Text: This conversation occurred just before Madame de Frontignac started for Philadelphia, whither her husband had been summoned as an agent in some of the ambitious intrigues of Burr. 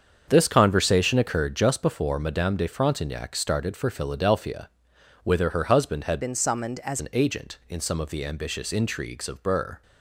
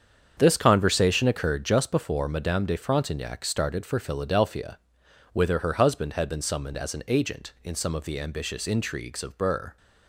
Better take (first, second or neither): second